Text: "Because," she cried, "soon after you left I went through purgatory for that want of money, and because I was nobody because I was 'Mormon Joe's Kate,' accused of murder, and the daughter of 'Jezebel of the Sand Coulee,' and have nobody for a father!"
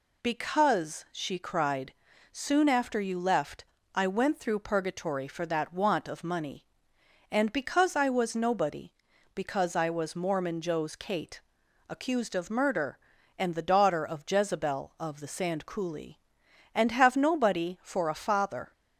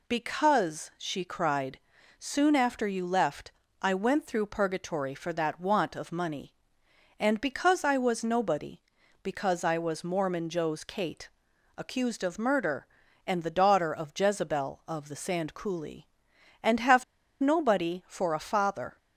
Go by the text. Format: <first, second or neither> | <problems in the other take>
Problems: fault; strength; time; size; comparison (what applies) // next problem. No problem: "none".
first | pauses between "left" and "I"; slight; at 3.4 s; 0.32 s long; slight in the first // pauses between "have" and "nobody"; at 17.0 s; 0.36 s long